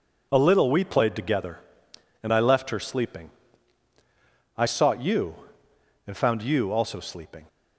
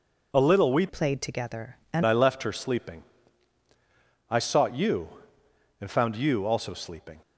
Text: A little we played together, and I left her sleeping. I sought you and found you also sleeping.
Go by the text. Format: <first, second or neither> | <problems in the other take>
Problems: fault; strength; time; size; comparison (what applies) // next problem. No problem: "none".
first | changes voice from "played" to "and"; from 0.8 to 2.0 s; 1.2 s long